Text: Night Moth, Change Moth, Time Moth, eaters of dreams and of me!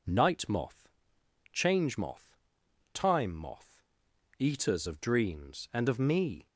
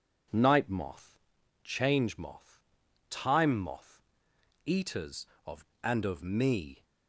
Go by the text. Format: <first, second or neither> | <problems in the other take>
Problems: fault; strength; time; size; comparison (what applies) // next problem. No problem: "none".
first | skips "dreams"; at 5.7 s